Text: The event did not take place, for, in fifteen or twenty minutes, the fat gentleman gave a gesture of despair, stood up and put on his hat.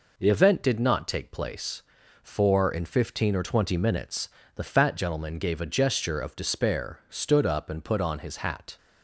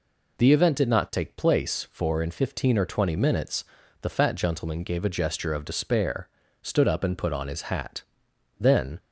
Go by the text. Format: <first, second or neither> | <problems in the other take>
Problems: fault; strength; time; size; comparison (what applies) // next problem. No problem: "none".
first | goes on to say "Then"; slight; from 8.5 s on; 0.40 s long